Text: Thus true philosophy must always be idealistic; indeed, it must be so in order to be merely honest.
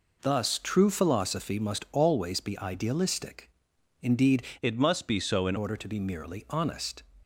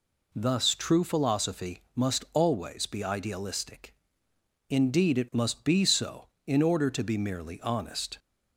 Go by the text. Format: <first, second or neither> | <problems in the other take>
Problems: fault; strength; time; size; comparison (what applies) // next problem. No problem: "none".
second | changes voice from "it" to "in"; from 4.6 to 5.5 s; 0.9 s long